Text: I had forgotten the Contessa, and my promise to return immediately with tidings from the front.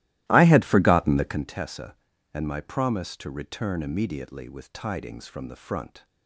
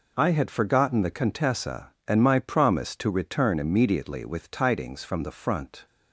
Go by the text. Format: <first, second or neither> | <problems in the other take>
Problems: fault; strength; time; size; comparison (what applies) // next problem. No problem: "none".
second | starts louder than the rest; strong; until 1.4 s; 16 dB